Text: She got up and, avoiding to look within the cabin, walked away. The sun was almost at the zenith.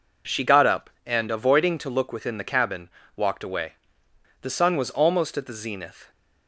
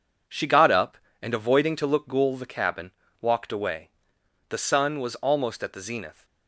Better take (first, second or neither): first